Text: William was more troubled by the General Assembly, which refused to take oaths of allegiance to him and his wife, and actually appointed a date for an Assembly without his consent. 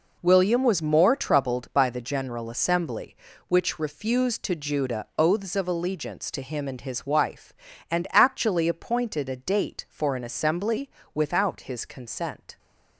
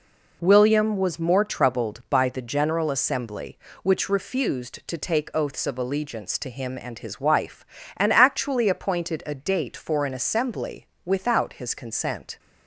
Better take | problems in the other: second | says "judah" for "take"; at 4.5 s // pauses between "Assembly" and "without"; slight; at 10.9 s; 0.24 s long; slight in the second

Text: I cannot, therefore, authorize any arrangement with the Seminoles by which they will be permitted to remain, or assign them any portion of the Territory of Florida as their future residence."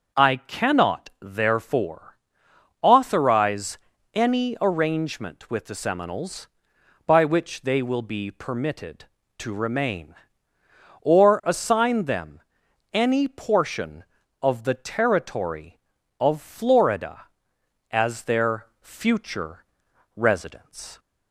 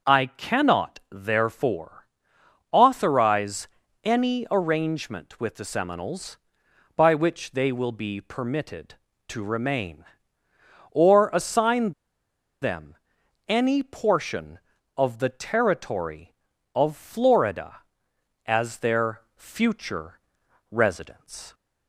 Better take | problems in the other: first | starts louder than the rest; noticeable; until 1.1 s; 6 dB; also in the first // pauses between "authorize" and "any"; slight; at 3.6 s; 0.36 s long; slight in the first // pauses between "assign" and "them"; noticeable; at 11.9 s; 0.70 s long // pauses between "them" and "any"; noticeable; at 12.9 s; 0.52 s long; noticeable in the first // pauses between "their" and "future"; slight; at 19.1 s; 0.16 s long; slight in the first // pauses between "future" and "residence"; noticeable; at 20.1 s; 0.50 s long; noticeable in the first

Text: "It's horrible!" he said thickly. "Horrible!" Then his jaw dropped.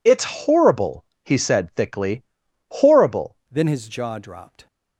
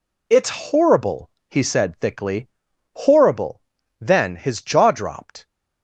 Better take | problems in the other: second | changes voice at "Then"; from 3.5 s on; 1.1 s long

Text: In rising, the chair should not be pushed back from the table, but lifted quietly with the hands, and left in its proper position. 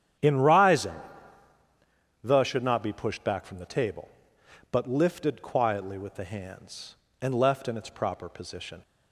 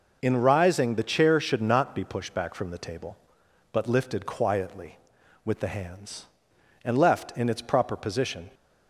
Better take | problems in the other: second | starts louder than the rest; strong; until 2.4 s; 10 dB // skips "chair"; at 2.4 s

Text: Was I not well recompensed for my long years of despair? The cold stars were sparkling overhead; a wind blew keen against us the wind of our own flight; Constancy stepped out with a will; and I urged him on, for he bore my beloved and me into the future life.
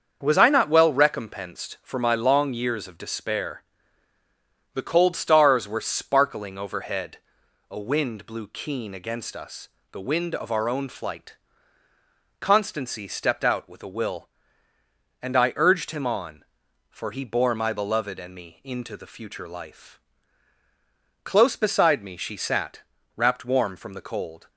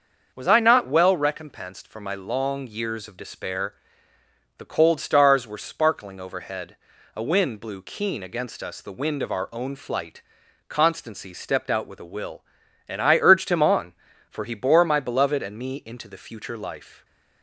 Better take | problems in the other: second | starts louder than the rest; until 1.2 s; 7 dB; also in the second // pauses between "us" and "the"; slight; at 9.6 s; 0.22 s long // goes on to say "Close beside me she sat wrapped warm from the cold"; strong; from 21.2 s on; 3.2 s long

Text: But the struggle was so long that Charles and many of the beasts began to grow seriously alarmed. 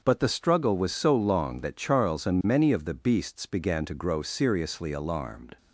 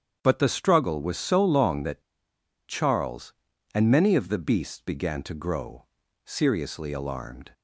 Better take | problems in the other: first | starts louder than the rest; strong; until 1.2 s; 8.5 dB // pauses between "that" and "Charles"; noticeable; at 2.0 s; 0.66 s long // pauses between "grow" and "seriously"; at 5.8 s; 0.38 s long

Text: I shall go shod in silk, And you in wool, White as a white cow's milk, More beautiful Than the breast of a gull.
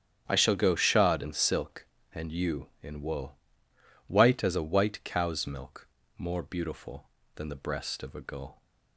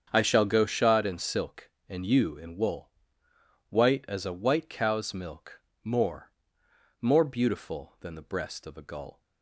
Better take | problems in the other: first | starts louder than the rest; strong; until 1.1 s; 7.5 dB; strong in the first // says "More" twice; at 7.0 s

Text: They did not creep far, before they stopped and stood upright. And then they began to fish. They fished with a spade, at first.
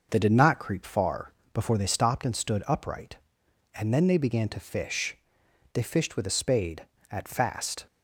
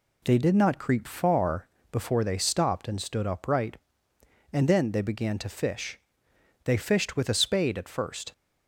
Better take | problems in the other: second | says "fast" for "first"; at 7.2 s

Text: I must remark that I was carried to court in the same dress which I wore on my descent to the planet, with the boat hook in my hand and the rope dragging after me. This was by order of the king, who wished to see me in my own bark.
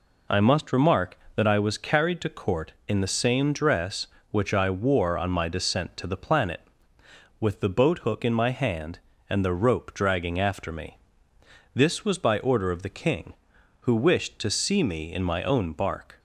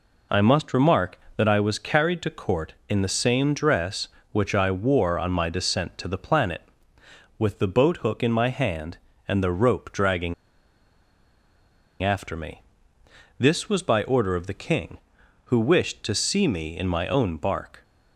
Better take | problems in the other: first | pauses between "dragging" and "after"; strong; at 10.3 s; 1.6 s long

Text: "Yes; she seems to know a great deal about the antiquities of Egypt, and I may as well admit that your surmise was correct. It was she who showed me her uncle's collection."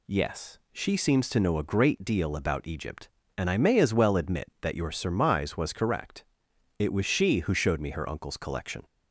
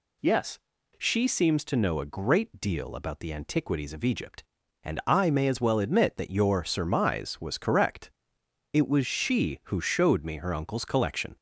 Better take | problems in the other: second | skips "the antiquities of"; at 2.6 s

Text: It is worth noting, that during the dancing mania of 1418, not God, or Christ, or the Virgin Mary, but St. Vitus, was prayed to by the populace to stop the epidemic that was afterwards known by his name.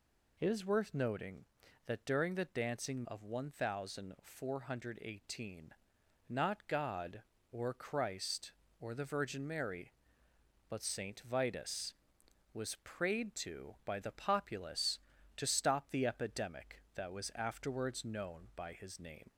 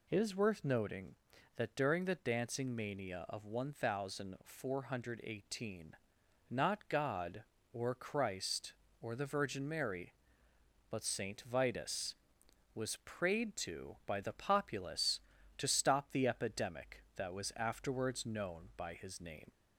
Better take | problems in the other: second | skips "mania"; at 3.0 s

